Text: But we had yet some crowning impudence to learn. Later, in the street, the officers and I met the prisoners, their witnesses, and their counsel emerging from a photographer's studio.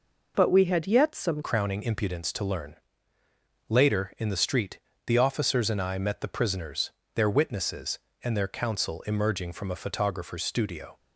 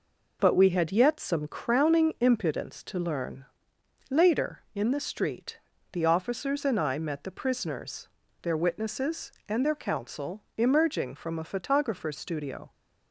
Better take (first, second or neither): second